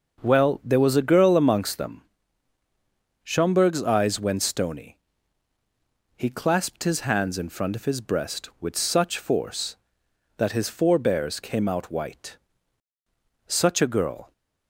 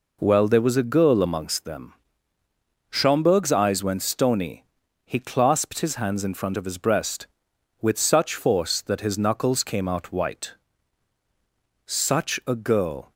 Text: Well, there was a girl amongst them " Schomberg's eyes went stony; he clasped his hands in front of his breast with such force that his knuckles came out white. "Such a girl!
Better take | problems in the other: second | starts louder than the rest; until 1.2 s; 6 dB // says "forebears" for "knuckles"; at 10.6 s

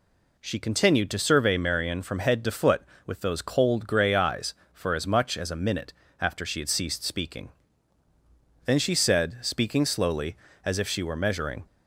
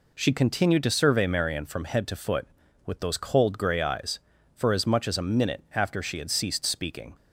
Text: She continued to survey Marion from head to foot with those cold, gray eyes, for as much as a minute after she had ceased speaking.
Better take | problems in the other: second | pauses between "minute" and "after"; slight; at 5.9 s; 0.28 s long // goes on to say "Then she said speaking slowly as if she were measuring"; strong; from 8.6 s on; 3.0 s long

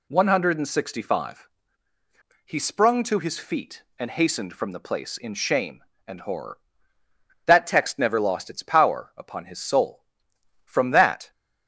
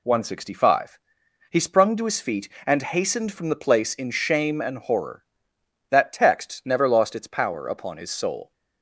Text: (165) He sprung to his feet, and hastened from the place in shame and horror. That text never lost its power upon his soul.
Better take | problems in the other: second | goes on to say "From that"; noticeable; from 10.6 s on; 0.66 s long

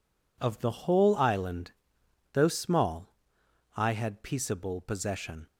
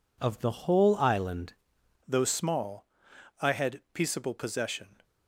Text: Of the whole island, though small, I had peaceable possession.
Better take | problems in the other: first | changes voice at "though"; from 2.0 s on; 3.0 s long

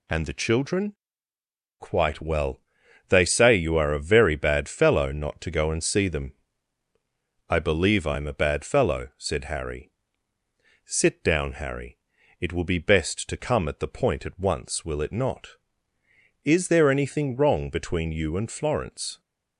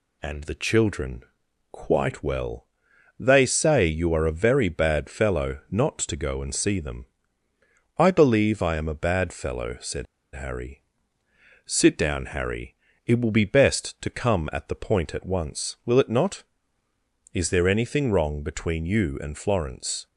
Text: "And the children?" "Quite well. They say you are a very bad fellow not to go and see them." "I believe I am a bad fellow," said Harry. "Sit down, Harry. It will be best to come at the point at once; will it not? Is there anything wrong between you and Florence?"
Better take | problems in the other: first | pauses between "said" and "Harry"; slight; at 10.0 s; 0.29 s long

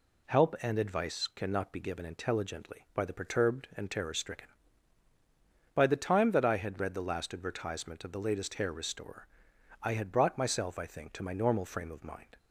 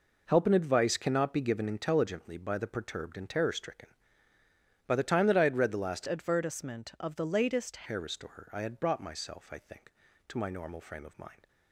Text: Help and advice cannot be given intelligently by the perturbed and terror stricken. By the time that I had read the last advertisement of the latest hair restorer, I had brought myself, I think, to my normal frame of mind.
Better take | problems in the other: first | changes voice from "advertisement" to "latest"; from 6.0 to 7.8 s; 1.8 s long

